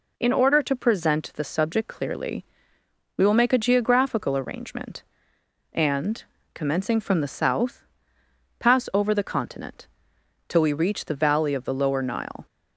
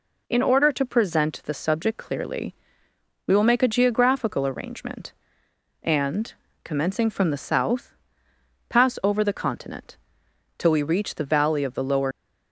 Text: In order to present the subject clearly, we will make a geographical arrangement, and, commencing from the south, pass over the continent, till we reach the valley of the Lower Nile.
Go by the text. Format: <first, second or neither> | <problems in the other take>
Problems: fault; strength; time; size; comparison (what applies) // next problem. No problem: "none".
first | stops before "Nile"; at 12.1 s